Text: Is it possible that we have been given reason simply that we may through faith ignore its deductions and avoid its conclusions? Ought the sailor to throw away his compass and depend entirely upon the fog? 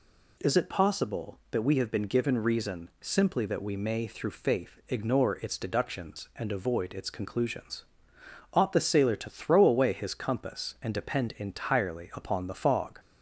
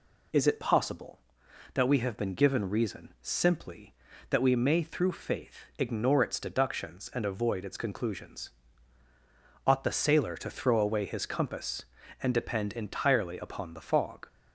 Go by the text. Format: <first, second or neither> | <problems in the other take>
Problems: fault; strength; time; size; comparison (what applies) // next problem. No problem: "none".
neither | none